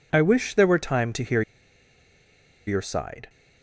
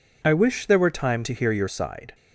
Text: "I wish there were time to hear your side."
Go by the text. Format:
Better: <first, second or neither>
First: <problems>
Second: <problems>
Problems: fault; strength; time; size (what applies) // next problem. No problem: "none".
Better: second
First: pauses between "hear" and "your"; strong; at 1.4 s; 1.2 s long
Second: none